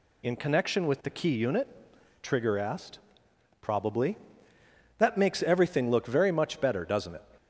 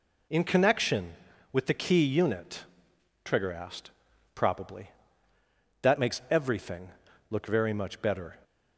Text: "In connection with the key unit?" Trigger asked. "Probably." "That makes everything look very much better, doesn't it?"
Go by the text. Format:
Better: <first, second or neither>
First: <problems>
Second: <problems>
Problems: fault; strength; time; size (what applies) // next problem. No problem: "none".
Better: first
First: none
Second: pauses between "everything" and "look"; at 6.8 s; 0.40 s long // stops before "doesn't it"; at 8.4 s